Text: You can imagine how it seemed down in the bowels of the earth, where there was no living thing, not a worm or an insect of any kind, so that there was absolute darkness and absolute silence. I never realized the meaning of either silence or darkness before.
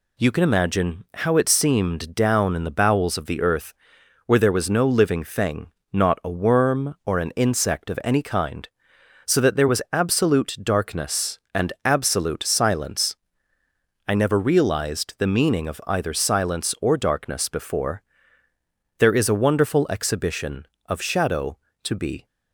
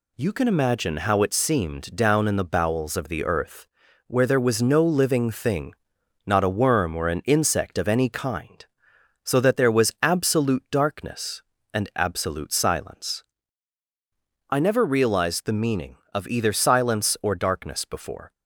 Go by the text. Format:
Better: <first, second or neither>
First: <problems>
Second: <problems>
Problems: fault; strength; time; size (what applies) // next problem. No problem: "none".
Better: second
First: goes on to say "There is a wonderful exhibition of shadow to be"; strong; from 18.9 s on; 3.2 s long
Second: none